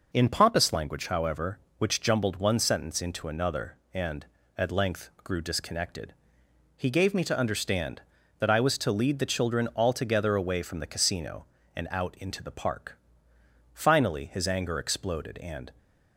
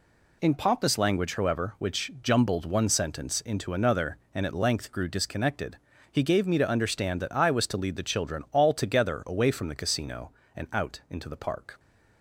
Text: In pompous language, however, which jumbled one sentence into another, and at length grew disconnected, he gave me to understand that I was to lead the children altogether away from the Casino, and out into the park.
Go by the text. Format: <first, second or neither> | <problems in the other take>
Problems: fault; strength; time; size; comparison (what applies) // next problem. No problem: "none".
second | pauses between "length" and "grew"; slight; at 5.0 s; 0.16 s long // goes on to say "Finally his anger exploded and"; strong; from 13.7 s on; 1.9 s long